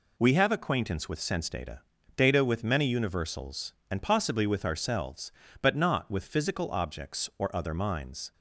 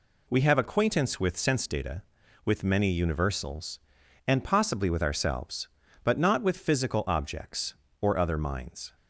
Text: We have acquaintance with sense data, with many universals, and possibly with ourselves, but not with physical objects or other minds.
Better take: second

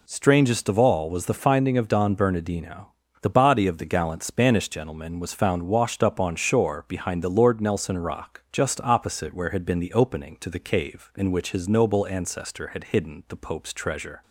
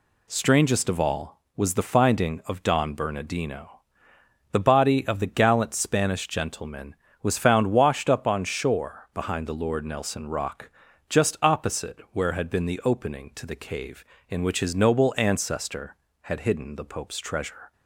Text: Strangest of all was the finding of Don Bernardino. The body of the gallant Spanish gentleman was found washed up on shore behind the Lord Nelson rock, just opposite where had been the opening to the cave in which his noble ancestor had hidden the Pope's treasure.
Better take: neither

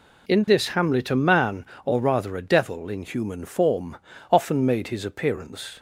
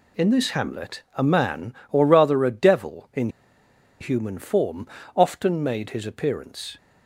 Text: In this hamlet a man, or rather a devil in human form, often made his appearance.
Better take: first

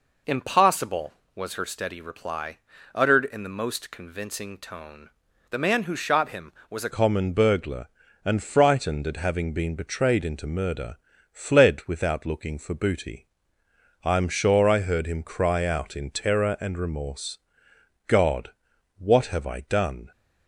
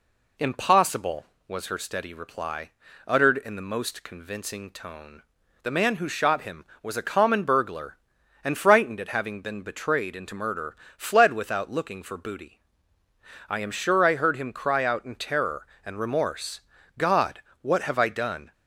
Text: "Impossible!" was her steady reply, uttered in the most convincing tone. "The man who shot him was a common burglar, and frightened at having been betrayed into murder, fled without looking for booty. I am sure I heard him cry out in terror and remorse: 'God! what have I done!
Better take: second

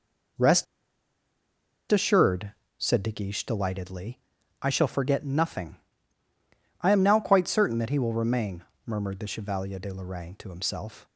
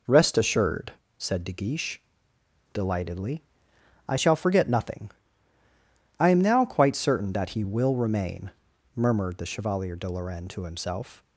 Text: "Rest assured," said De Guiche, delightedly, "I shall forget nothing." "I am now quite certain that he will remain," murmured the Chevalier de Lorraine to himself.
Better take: second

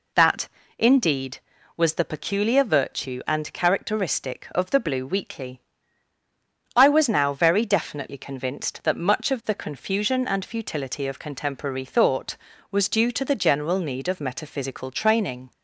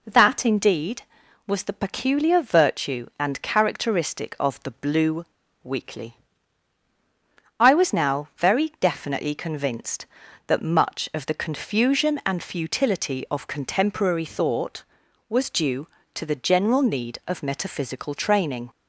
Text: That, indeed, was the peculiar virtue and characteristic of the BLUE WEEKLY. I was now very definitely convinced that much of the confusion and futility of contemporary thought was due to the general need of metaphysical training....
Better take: first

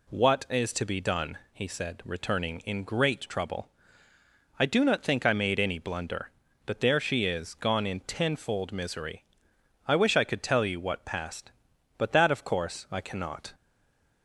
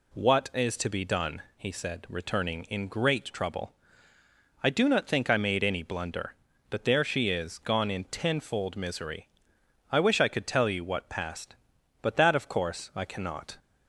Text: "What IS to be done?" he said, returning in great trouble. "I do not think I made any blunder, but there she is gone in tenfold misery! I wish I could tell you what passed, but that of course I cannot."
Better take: second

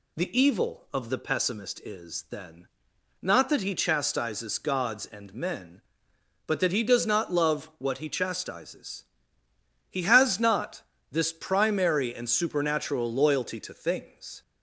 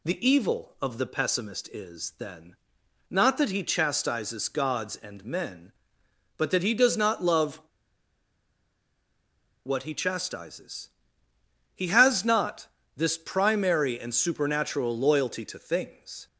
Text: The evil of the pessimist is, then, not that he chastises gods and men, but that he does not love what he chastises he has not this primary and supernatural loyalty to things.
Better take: first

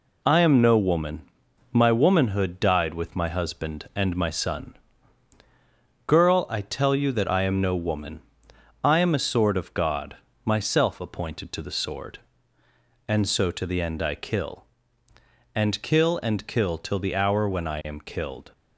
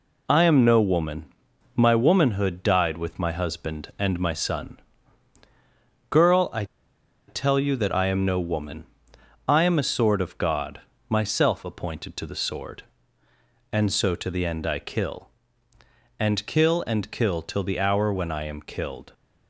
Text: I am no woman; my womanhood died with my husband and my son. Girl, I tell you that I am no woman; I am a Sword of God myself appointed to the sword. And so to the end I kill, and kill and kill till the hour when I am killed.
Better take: first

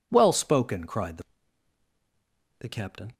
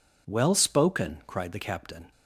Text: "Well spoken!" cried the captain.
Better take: second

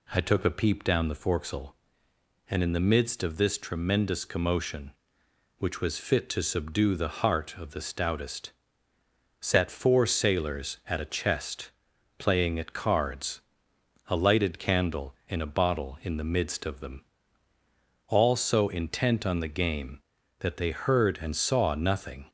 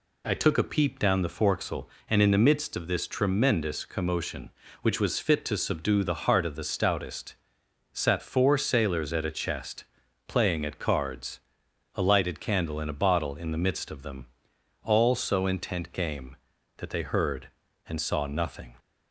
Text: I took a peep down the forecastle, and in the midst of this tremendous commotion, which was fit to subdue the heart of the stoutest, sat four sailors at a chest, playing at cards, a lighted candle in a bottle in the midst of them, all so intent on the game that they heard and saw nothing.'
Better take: first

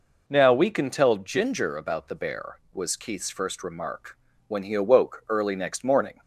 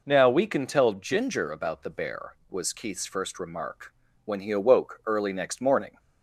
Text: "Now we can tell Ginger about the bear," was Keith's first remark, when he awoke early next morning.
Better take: neither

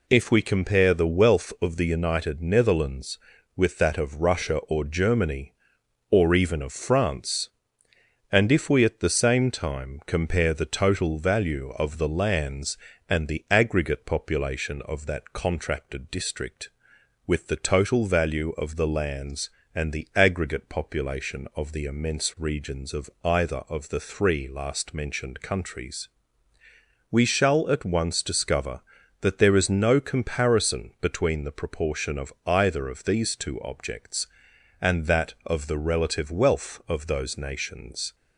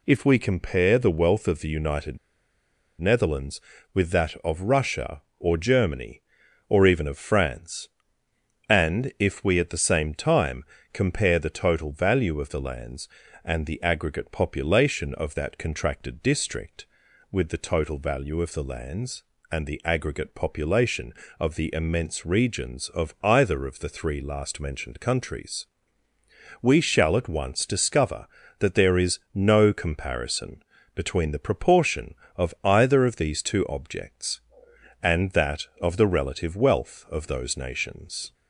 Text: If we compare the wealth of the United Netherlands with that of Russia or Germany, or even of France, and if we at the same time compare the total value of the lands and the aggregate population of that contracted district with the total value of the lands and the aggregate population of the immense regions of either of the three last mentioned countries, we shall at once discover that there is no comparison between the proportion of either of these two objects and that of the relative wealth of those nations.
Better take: first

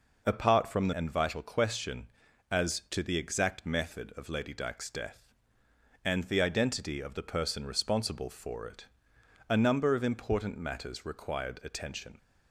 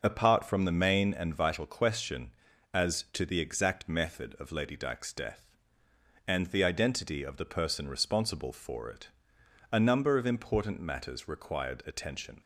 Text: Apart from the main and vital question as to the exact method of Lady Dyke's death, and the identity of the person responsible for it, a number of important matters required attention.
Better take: second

